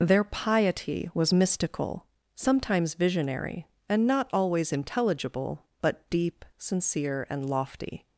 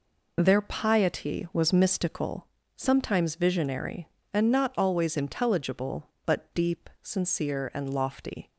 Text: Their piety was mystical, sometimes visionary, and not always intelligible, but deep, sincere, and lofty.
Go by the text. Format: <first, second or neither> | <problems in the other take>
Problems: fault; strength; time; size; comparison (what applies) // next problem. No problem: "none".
neither | none